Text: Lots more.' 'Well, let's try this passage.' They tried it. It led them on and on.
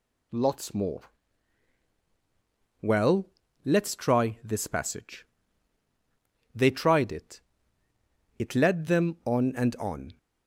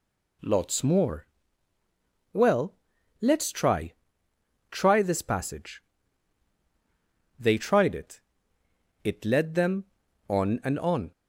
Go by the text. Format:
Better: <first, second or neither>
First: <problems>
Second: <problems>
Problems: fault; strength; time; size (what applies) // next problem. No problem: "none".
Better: first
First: none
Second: says "try" twice; at 4.7 s